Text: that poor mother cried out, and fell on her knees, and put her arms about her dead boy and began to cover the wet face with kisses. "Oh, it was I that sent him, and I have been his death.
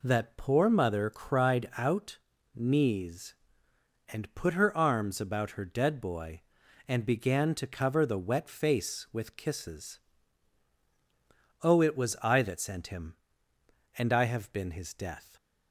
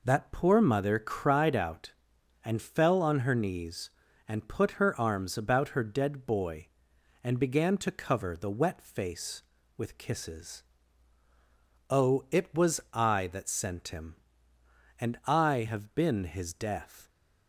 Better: second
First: skips "and fell on her"; at 2.3 s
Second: none

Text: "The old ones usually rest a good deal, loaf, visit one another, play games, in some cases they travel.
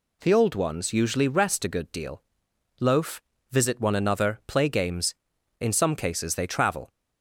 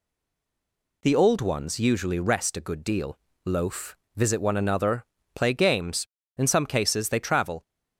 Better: first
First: none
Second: stays silent before the first word; until 1.0 s; 1.0 s long

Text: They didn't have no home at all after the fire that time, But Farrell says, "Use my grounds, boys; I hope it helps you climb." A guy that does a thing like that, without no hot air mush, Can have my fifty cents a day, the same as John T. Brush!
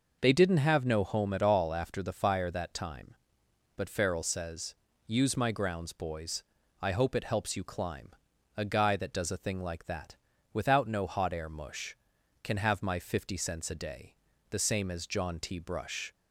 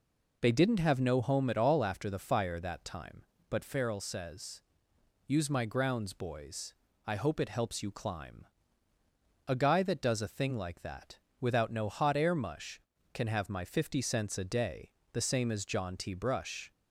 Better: neither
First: none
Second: none

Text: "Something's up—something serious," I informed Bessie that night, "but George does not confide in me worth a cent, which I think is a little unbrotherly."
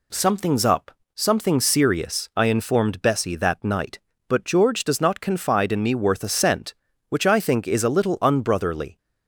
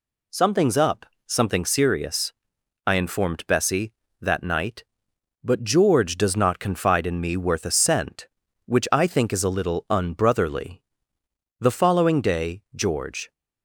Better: first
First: none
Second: goes on to say "The following day George"; strong; from 11.5 s on; 1.7 s long

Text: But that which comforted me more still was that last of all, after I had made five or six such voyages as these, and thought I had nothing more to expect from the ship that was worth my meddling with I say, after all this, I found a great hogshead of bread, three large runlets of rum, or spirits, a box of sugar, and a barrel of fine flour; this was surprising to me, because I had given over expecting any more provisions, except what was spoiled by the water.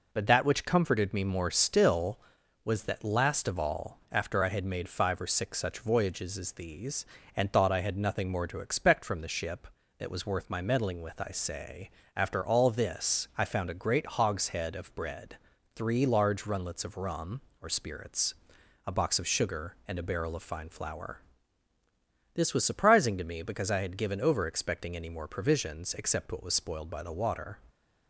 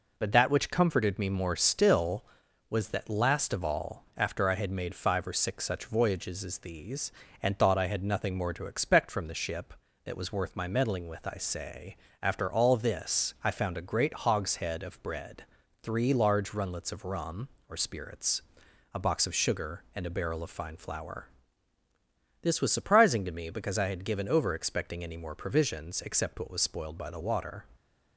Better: neither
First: none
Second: none

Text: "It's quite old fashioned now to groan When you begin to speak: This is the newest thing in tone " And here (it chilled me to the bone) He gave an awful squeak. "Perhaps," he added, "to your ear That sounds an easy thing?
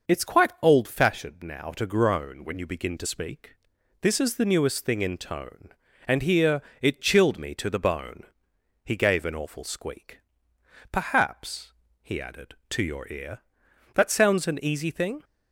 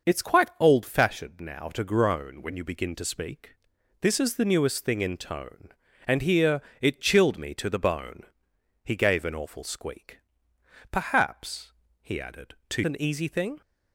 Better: first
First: none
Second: skips "your ear That sounds"; at 12.8 s

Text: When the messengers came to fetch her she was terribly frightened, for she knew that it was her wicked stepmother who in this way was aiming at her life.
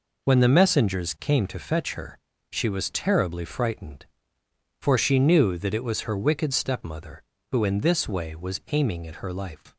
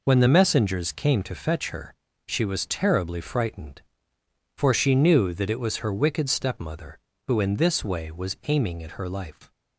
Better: neither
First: pauses between "her" and "she"; slight; at 2.1 s; 0.32 s long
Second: pauses between "her" and "she"; slight; at 1.9 s; 0.32 s long

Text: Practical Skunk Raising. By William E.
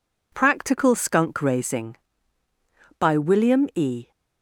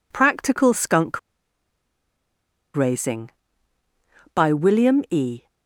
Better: first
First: none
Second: pauses between "Skunk" and "Raising"; strong; at 1.1 s; 1.5 s long

